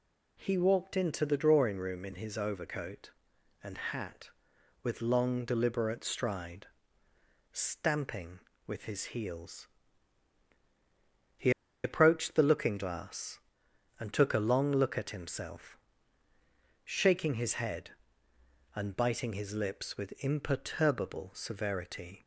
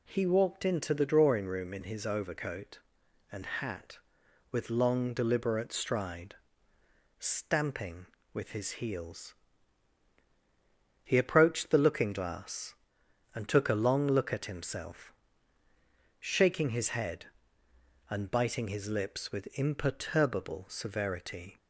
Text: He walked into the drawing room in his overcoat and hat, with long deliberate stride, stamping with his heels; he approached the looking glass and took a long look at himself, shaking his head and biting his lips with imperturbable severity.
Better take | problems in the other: second | pauses between "he" and "approached"; slight; at 11.5 s; 0.33 s long

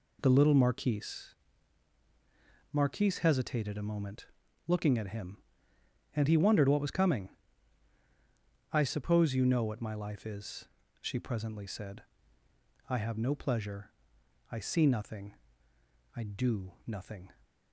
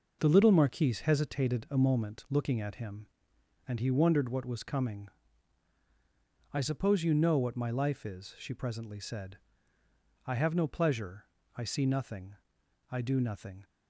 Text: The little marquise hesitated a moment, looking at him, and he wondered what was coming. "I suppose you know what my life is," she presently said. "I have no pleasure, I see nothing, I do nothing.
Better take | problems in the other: second | says "marquise" twice; at 2.7 s

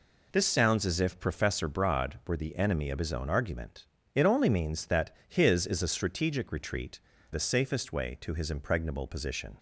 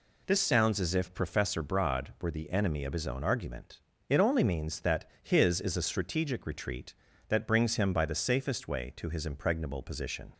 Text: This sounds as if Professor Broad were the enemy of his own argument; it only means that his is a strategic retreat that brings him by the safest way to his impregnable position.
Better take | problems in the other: second | skips "that brings him by"; at 7.1 s

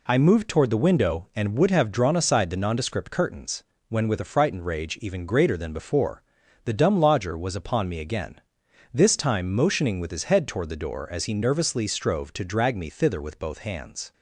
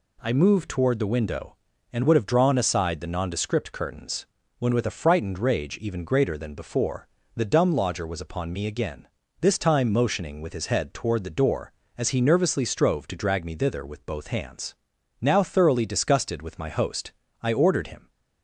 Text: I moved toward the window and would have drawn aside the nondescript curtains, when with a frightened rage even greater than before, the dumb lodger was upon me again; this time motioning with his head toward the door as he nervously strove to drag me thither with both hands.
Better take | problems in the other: first | goes on to say "Now thoroughly disgusted with my host I ordered him"; strong; from 15.2 s on; 2.8 s long

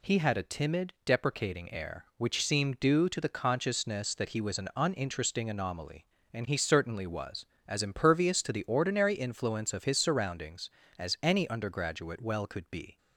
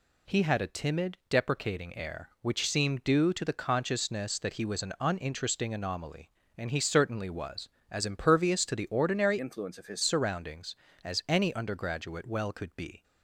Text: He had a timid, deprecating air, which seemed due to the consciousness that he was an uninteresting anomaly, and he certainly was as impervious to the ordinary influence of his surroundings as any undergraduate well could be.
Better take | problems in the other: first | changes voice from "influence" to "his"; from 9.4 to 10.0 s; 0.6 s long

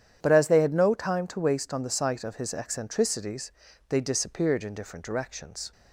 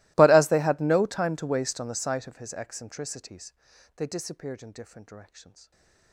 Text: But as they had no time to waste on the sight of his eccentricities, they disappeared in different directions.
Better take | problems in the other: first | gets quieter; strong; throughout; 29.5 dB // starts louder than the rest; strong; until 1.1 s; 21 dB; strong in the first // stays silent after the last word; slight; from 5.6 s on; 0.5 s long

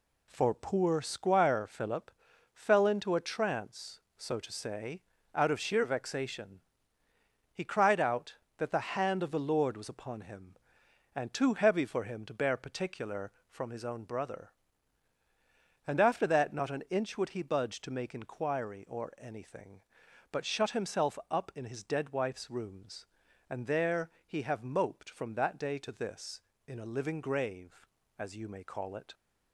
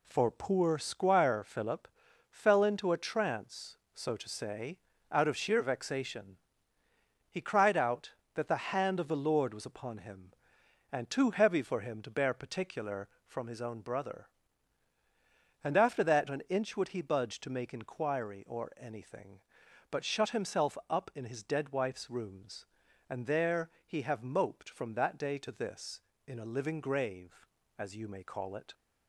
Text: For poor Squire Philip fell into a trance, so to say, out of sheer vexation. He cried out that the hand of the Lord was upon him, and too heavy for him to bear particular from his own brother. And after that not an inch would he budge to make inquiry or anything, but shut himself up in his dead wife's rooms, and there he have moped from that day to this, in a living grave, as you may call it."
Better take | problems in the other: first | pauses between "Philip" and "fell"; at 1.8 s; 0.42 s long; also in the first // skips "not"; at 16.2 s // pauses between "there" and "he"; slight; at 23.6 s; 0.16 s long; slight in the first

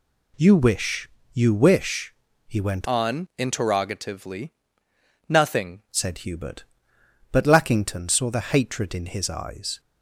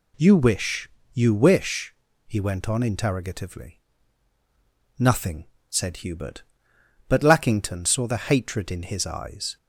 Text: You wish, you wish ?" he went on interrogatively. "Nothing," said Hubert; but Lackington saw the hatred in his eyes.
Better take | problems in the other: second | changes voice from "on" to "Nothing"; from 2.8 to 5.8 s; 3.0 s long

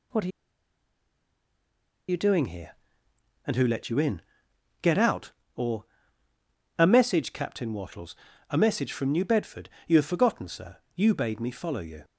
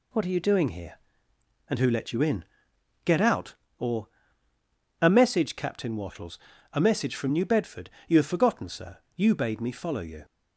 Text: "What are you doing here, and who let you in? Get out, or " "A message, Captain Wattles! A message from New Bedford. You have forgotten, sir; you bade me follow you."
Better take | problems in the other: second | pauses between "are" and "you"; strong; at 0.3 s; 1.7 s long

